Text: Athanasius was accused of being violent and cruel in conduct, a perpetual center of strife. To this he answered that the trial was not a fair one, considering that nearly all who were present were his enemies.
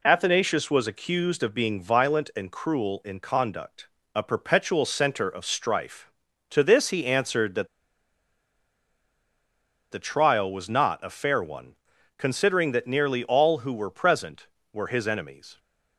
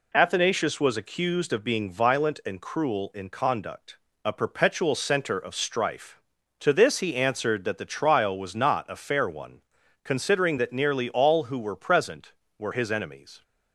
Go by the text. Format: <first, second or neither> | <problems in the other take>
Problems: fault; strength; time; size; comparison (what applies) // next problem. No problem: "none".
second | pauses between "that" and "the"; strong; at 7.6 s; 2.2 s long